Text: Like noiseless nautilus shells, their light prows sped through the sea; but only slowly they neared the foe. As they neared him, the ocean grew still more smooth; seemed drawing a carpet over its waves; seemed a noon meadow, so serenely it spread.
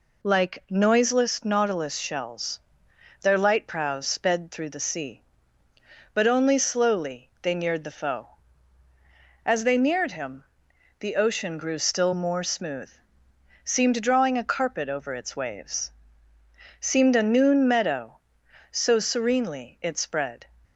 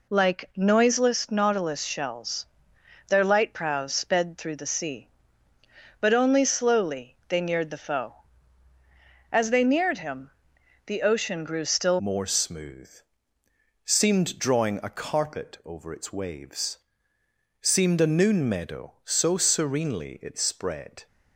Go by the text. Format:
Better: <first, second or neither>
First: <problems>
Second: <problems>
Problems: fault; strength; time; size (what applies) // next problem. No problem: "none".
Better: first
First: none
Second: changes voice at "more"; from 11.9 s on; 9.1 s long